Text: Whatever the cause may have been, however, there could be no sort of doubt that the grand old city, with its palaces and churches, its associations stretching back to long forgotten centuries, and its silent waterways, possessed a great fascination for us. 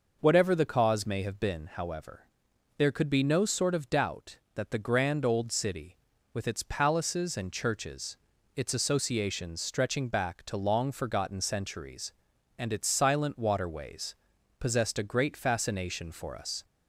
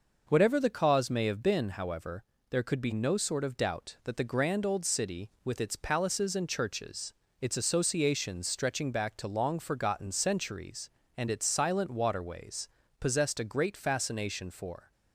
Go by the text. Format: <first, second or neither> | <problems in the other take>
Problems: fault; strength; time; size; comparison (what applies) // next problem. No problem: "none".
first | stops before "us"; at 14.9 s